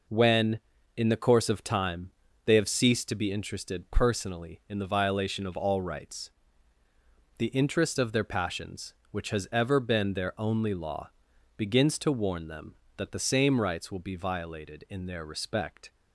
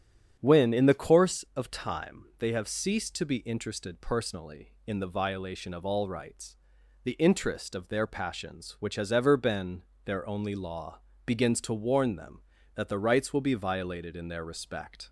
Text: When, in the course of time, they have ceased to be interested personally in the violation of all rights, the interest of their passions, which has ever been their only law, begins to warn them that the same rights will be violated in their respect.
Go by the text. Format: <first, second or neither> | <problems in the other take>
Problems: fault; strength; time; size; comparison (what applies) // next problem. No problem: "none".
first | starts louder than the rest; strong; until 1.4 s; 9 dB // pauses between "been" and "their"; slight; at 9.8 s; 0.24 s long // skips "same"; at 12.9 s